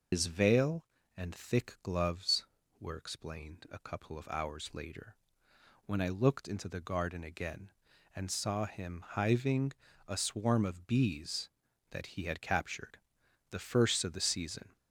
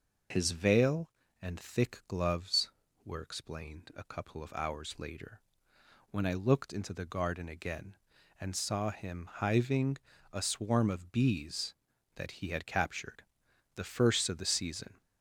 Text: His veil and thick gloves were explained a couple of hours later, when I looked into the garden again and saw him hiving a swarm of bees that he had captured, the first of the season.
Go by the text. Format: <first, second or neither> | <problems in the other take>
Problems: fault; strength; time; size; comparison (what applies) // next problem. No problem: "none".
second | loses the start of "His"; at 0.1 s; 70 ms // pauses between "hiving" and "a"; slight; at 9.7 s; 0.34 s long; slight in the second